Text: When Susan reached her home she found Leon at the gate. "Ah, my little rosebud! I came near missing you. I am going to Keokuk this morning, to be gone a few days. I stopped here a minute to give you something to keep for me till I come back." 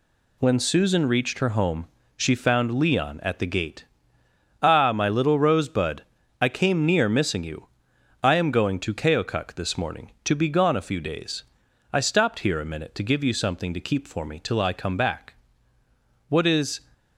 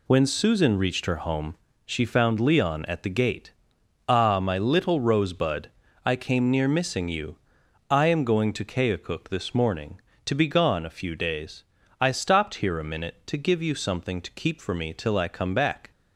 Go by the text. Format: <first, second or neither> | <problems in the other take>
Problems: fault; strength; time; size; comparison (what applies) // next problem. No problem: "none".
second | pauses between "home" and "she"; slight; at 1.8 s; 0.28 s long; slight in the second // goes on to say "What is"; from 16.2 s on; 0.50 s long